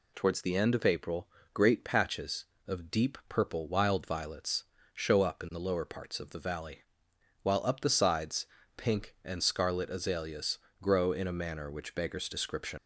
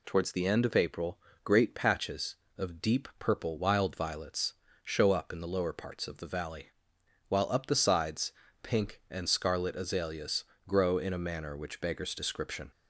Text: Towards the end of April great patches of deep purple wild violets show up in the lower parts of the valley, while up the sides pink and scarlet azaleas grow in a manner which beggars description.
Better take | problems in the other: second | pauses between "April" and "great"; slight; at 1.2 s; 0.24 s long; slight in the second // pauses between "violets" and "show"; slight; at 4.6 s; 0.28 s long; slight in the second // pauses between "sides" and "pink"; slight; at 8.4 s; 0.30 s long; slight in the second // pauses between "azaleas" and "grow"; slight; at 10.5 s; 0.22 s long; slight in the second // leaves "description" unfinished; at 12.7 s; 70 ms

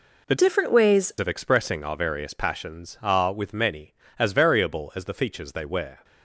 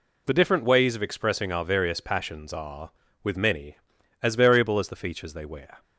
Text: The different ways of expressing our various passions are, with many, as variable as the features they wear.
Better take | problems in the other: second | changes voice from "different" to "ways"; from 0.3 to 1.1 s; 0.8 s long

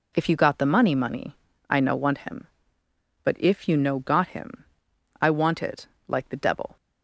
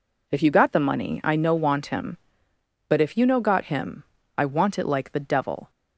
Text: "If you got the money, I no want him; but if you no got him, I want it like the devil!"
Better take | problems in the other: second | says "money" twice; at 0.9 s // pauses between "it" and "like"; slight; at 5.8 s; 0.22 s long

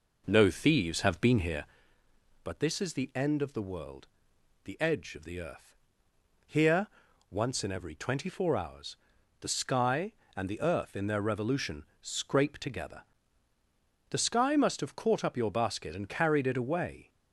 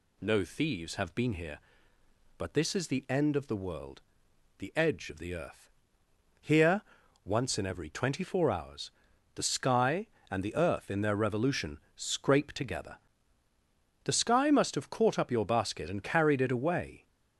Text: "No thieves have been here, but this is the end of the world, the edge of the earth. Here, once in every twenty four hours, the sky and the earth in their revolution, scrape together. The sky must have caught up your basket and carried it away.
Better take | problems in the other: second | starts louder than the rest; noticeable; until 1.8 s; 5 dB

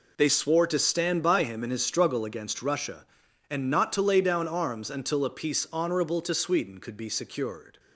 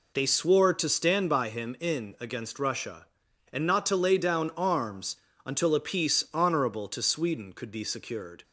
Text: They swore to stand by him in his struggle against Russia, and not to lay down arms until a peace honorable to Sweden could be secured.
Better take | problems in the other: first | skips "his struggle"; at 2.1 s // pauses between "arms" and "until"; slight; at 5.1 s; 0.28 s long

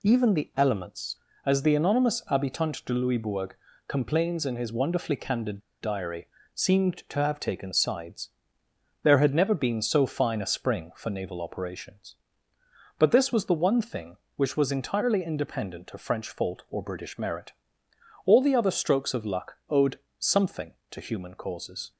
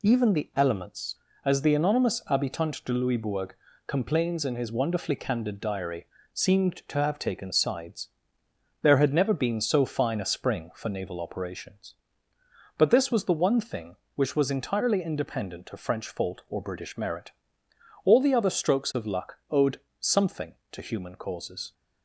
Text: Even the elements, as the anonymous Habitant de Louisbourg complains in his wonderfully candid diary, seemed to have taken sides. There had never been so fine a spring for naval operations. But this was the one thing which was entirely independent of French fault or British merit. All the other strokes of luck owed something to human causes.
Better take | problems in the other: second | pauses between "Louisbourg" and "complains"; slight; at 3.5 s; 0.32 s long; slight in the second // pauses between "candid" and "diary"; slight; at 5.5 s; 0.22 s long // pauses between "owed" and "something"; slight; at 19.9 s; 0.18 s long; slight in the second

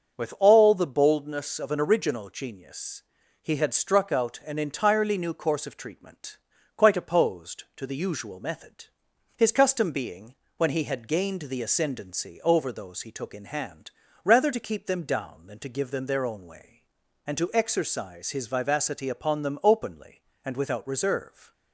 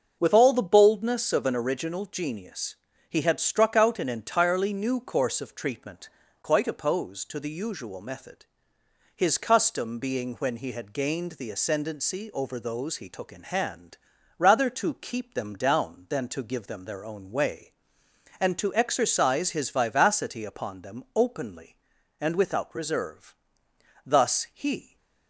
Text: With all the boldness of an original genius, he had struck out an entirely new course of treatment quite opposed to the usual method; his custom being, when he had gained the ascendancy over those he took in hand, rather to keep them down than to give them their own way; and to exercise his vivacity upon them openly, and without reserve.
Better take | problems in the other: first | starts louder than the rest; until 1.2 s; 6 dB; noticeable in the first // pauses between "treatment" and "quite"; slight; at 6.0 s; 0.34 s long; also in the first // goes on to say "Thus he"; noticeable; from 24.0 s on; 0.92 s long

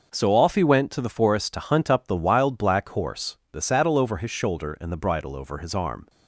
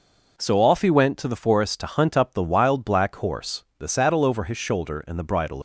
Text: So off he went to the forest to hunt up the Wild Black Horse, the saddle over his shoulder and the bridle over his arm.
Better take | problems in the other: first | stops before "over his arm"; at 5.5 s

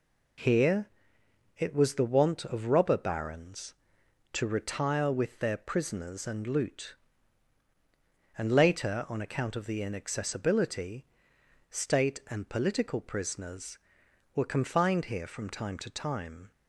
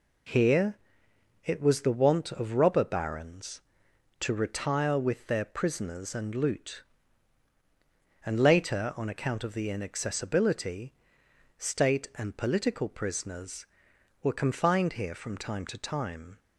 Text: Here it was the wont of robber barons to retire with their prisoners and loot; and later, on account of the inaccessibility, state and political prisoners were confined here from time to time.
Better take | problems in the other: neither | pauses between "Here" and "it"; noticeable; the same in both

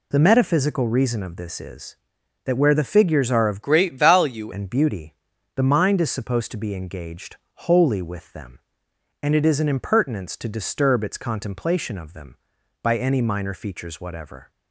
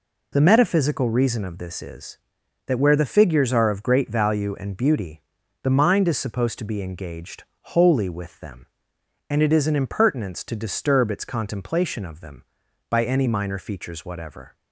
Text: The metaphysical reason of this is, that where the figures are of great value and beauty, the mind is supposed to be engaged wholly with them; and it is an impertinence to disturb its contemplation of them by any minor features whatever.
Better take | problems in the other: second | changes voice from "great" to "value"; from 3.6 to 4.5 s; 0.9 s long // pauses between "engaged" and "wholly"; slight; at 7.3 s; 0.18 s long; slight in the second

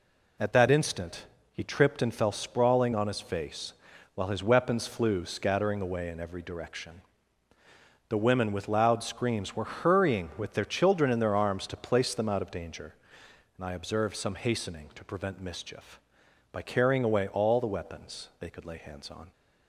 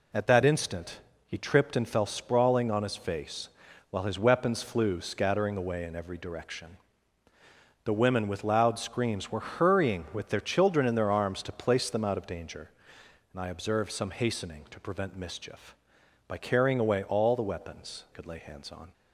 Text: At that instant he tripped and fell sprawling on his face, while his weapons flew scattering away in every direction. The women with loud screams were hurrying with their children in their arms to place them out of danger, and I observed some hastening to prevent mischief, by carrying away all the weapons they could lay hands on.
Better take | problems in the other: first | pauses between "instant" and "he"; slight; at 0.9 s; 0.26 s long; slight in the first // skips "they"; at 18.0 s

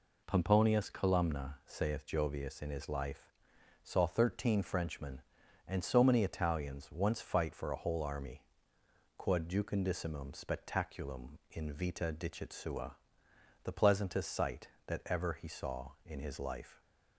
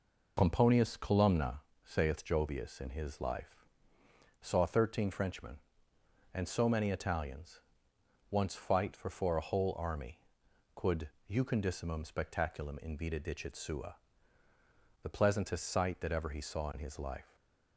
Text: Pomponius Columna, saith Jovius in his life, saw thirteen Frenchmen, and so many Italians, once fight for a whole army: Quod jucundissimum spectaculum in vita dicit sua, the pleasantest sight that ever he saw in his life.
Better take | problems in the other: first | says "for" twice; at 9.1 s // pauses between "Quod" and "jucundissimum"; slight; at 11.0 s; 0.20 s long // stays silent after the last word; slight; from 17.2 s on; 0.5 s long

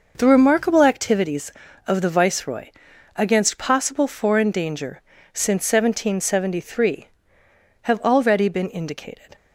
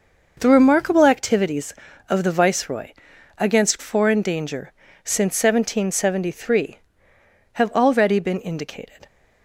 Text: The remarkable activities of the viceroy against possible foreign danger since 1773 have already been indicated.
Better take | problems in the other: first | pauses between "viceroy" and "against"; noticeable; at 2.9 s; 0.46 s long; noticeable in the first // skips "possible"; at 3.7 s // pauses between "danger" and "since"; slight; at 4.7 s; 0.32 s long; slight in the first

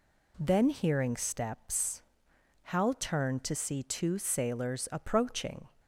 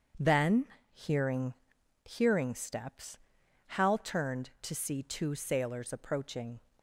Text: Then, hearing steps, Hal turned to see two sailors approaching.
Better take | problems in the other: first | says "hearing" twice; at 2.0 s

